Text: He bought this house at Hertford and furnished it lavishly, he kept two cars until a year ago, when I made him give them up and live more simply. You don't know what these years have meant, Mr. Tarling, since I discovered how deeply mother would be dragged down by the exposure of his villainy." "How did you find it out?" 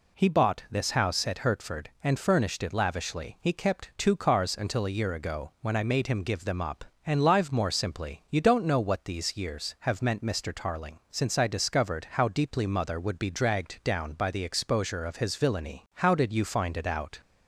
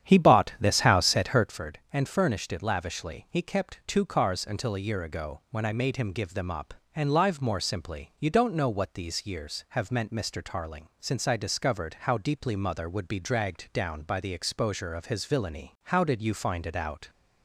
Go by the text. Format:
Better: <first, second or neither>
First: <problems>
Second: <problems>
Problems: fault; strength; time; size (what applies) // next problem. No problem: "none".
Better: first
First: none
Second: starts louder than the rest; strong; until 1.6 s; 9.5 dB